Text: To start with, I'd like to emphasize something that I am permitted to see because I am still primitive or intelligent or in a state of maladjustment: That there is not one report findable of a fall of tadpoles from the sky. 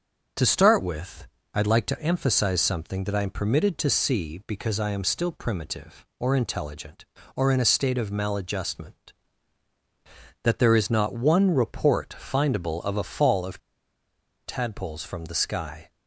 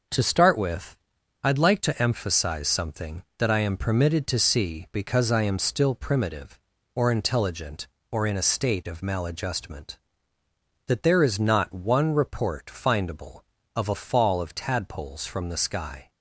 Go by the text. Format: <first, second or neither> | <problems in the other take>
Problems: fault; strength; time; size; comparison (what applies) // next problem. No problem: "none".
second | starts louder than the rest; until 1.6 s; 6.5 dB // pauses between "of" and "tadpoles"; noticeable; at 13.5 s; 0.87 s long